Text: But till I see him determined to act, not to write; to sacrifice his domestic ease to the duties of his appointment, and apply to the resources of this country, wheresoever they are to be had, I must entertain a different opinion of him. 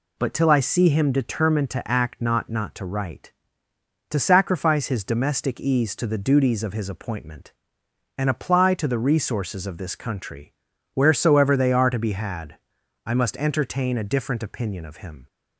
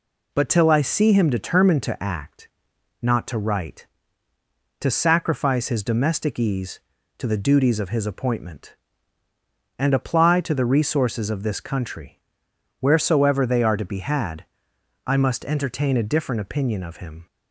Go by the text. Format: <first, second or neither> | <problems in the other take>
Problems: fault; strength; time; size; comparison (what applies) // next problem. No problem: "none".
second | says "not" twice; at 2.4 s